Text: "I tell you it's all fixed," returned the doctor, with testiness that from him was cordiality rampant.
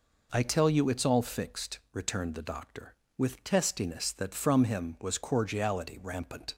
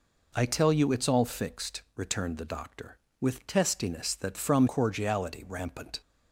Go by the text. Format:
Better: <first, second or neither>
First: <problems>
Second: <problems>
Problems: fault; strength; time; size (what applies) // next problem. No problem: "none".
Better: first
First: none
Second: skips "him was"; at 4.6 s